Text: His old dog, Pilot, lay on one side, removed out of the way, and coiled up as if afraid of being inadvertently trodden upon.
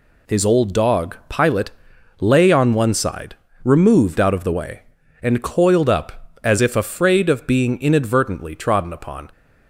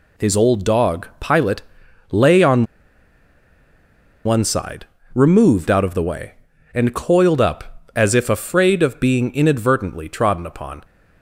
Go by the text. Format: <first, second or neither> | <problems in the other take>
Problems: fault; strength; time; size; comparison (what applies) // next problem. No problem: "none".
first | pauses between "on" and "one"; strong; at 2.6 s; 1.6 s long